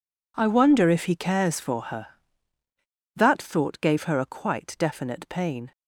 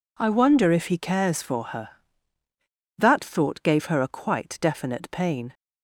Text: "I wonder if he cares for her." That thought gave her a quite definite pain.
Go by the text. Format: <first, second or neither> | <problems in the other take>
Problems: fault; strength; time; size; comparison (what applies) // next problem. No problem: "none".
second | gets quieter; strong; throughout; 16 dB